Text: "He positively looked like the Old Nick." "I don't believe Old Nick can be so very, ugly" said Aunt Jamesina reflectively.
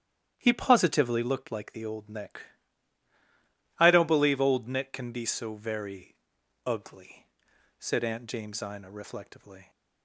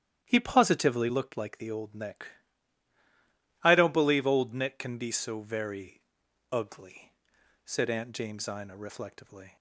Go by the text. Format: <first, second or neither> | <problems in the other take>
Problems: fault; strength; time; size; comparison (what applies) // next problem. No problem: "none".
neither | starts louder than the rest; strong; the same in both // pauses between "ugly" and "said"; noticeable; the same in both